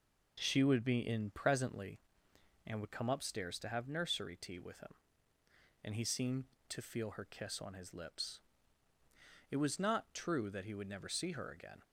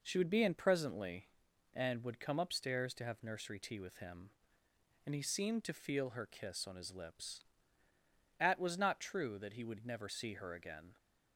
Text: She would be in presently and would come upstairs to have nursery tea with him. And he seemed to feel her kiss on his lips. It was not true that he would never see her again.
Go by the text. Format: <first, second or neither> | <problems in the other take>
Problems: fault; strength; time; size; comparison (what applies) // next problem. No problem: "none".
first | says "At" for "It"; at 8.3 s